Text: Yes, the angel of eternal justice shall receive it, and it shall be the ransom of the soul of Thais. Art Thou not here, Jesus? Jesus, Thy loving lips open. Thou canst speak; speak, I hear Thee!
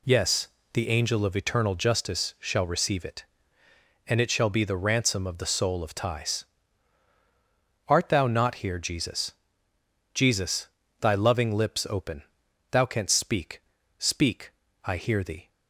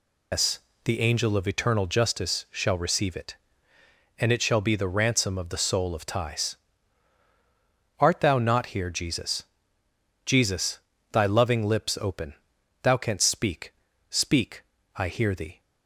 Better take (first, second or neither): first